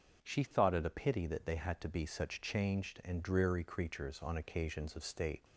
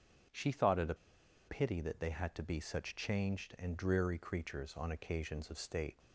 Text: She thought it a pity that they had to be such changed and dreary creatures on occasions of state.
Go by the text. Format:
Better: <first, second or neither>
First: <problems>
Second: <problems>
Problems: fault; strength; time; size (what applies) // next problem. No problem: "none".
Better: first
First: starts louder than the rest; until 1.2 s; 6.5 dB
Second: starts louder than the rest; until 1.8 s; 6.5 dB // pauses between "a" and "pity"; noticeable; at 0.9 s; 0.52 s long